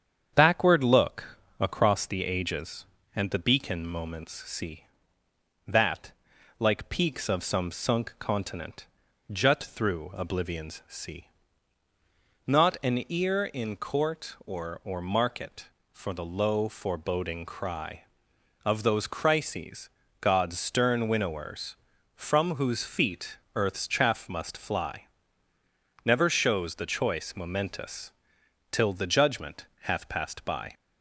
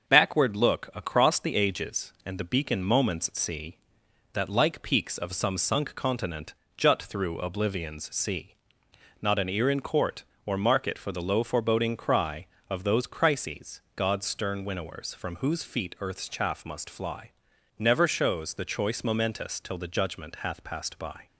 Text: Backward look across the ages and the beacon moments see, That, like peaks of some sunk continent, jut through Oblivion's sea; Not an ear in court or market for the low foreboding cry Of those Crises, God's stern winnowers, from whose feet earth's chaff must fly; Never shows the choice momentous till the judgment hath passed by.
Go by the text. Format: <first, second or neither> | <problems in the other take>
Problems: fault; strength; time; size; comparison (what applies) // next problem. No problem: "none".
second | starts louder than the rest; strong; until 1.3 s; 8 dB; also in the second // pauses between "look" and "across"; slight; at 1.3 s; 0.22 s long // says "or" twice; at 14.8 s // pauses between "feet" and "earth's"; slight; at 23.3 s; 0.16 s long // pauses between "momentous" and "till"; noticeable; at 28.0 s; 0.62 s long